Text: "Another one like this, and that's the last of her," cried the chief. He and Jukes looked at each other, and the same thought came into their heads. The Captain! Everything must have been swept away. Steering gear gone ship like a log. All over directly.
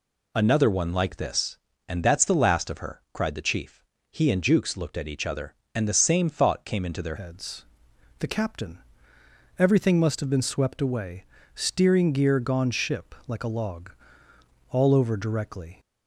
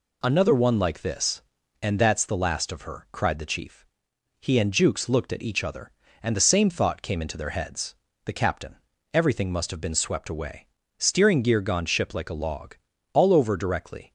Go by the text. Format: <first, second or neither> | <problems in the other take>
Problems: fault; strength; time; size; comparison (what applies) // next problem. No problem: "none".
second | changes voice at "heads"; from 7.1 s on; 8.6 s long